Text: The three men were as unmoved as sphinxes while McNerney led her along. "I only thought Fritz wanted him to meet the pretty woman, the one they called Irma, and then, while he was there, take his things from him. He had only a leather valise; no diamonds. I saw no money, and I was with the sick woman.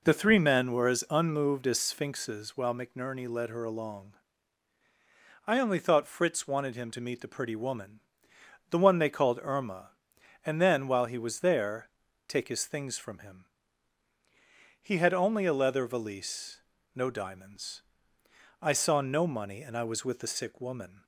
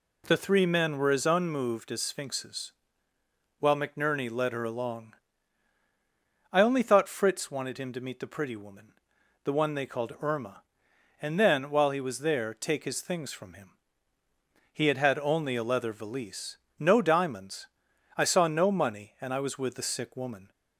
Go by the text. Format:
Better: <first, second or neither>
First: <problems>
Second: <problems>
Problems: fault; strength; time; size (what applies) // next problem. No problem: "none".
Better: first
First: none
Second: pauses between "sphinxes" and "while"; noticeable; at 2.7 s; 0.88 s long // says "had" twice; at 14.9 s